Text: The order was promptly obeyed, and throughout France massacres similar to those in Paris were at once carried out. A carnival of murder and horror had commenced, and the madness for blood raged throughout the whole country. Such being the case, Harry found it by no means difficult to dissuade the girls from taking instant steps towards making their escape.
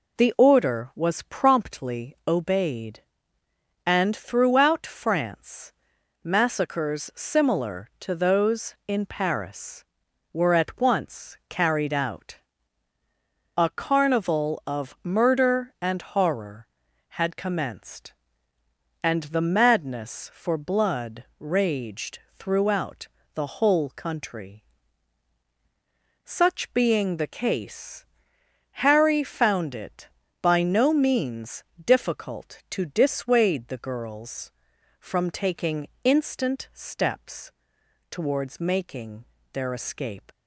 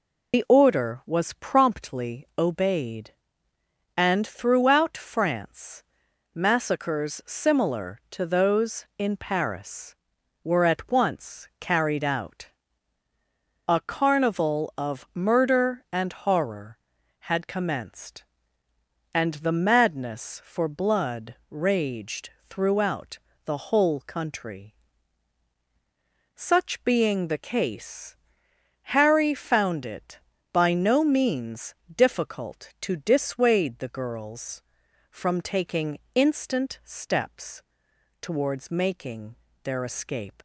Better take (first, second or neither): first